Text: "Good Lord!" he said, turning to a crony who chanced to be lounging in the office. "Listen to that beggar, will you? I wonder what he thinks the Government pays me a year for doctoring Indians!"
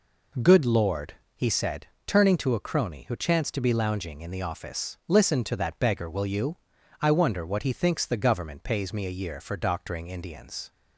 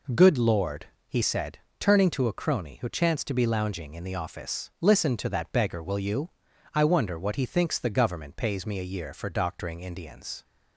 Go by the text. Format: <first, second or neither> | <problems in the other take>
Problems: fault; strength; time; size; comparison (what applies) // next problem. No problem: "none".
neither | none